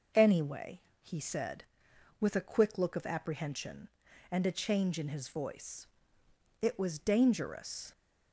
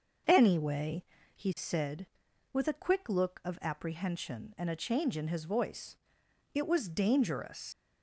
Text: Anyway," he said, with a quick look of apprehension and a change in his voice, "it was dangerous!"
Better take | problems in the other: first | starts louder than the rest; until 1.6 s; 6.5 dB // leaves "dangerous" unfinished; at 7.7 s; 115 ms

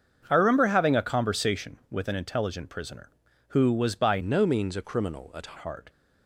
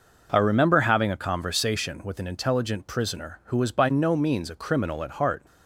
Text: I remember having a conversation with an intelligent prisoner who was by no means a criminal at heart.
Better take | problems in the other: second | starts louder than the rest; until 1.3 s; 7 dB // changes voice from "no" to "at"; from 4.2 to 5.5 s; 1.3 s long

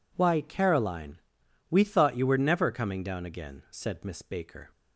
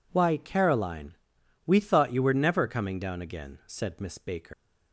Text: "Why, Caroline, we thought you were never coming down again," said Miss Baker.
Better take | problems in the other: first | leaves "Baker" unfinished; at 4.5 s; 130 ms

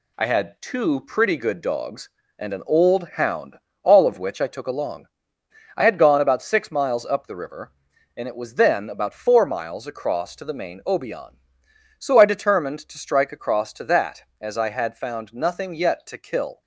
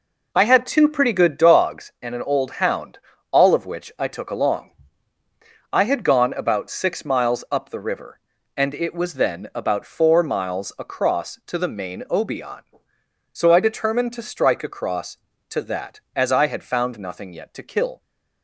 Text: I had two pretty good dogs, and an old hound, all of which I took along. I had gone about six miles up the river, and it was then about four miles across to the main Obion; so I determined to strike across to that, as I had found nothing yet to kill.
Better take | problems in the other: neither | none

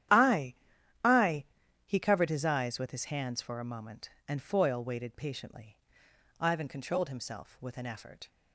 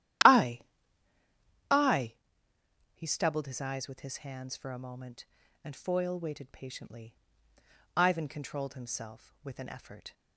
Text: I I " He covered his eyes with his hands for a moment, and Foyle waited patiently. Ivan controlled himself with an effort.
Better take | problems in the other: first | starts louder than the rest; strong; until 2.7 s; 12.5 dB; strong in the first // pauses between "I" and "I"; at 0.6 s; 1.1 s long; noticeable in the first // says "stubbled" for "covered"; at 3.0 s

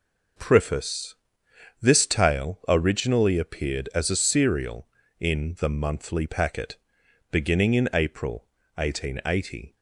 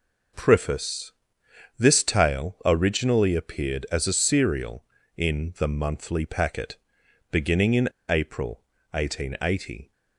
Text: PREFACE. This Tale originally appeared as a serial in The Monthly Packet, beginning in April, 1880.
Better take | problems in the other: first | pauses between "in" and "April"; slight; at 7.8 s; 0.20 s long

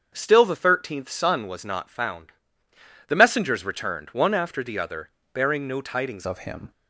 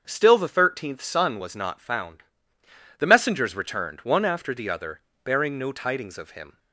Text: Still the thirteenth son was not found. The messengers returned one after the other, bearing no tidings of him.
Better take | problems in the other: second | starts louder than the rest; until 1.1 s; 7 dB; also in the second // changes voice at "of"; from 6.2 s on; 0.5 s long

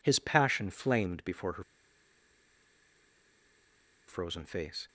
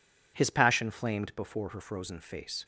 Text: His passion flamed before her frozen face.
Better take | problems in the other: second | pauses between "her" and "frozen"; strong; at 1.6 s; 2.4 s long

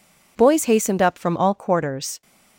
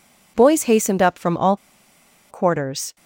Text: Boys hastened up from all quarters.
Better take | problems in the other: first | pauses between "all" and "quarters"; noticeable; at 1.5 s; 0.74 s long

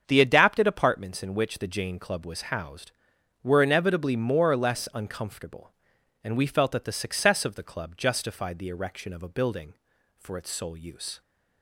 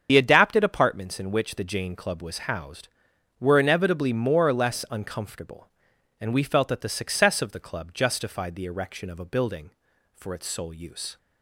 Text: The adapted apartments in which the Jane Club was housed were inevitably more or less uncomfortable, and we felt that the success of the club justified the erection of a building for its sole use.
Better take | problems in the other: first | loses the start of "The"; at 0.0 s; 65 ms // starts louder than the rest; strong; until 1.1 s; 7.5 dB; strong in the first

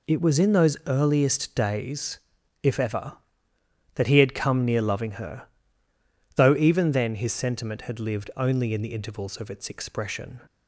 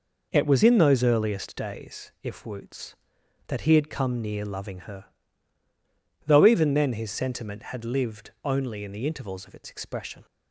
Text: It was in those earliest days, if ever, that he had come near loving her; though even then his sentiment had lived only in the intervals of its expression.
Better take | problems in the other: first | says "woots" for "ever"; at 2.4 s

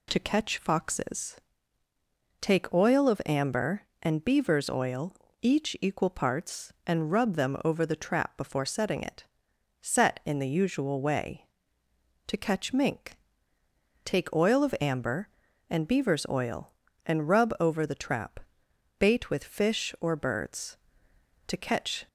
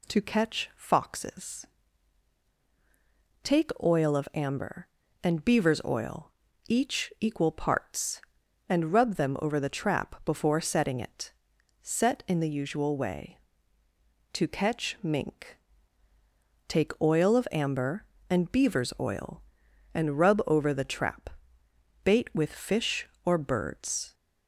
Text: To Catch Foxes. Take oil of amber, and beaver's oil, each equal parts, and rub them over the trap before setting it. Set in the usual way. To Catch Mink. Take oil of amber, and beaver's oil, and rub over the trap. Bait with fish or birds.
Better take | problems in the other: second | goes on to say "To Catch"; from 21.4 s on; 0.58 s long

